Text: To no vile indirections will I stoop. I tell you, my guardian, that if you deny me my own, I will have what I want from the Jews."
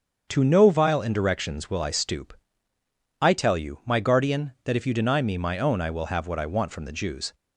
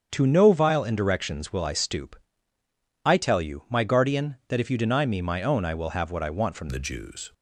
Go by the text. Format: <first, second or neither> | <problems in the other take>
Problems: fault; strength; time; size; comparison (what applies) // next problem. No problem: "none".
first | starts louder than the rest; strong; until 1.1 s; 7.5 dB; also in the first // changes voice at "the"; from 6.6 s on; 0.7 s long